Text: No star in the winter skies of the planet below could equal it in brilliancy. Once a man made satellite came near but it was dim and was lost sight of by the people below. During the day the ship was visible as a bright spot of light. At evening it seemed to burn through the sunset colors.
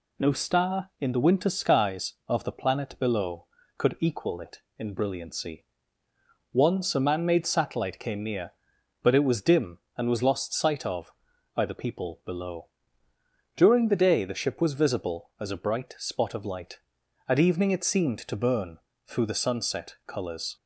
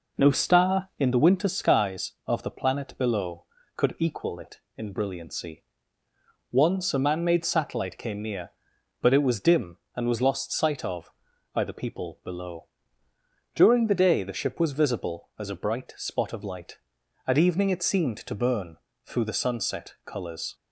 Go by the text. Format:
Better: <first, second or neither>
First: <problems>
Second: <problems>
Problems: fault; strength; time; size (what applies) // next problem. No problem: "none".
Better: first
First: pauses between "burn" and "through"; slight; at 18.7 s; 0.28 s long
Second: starts louder than the rest; noticeable; until 1.4 s; 5 dB // pauses between "burn" and "through"; slight; at 18.7 s; 0.28 s long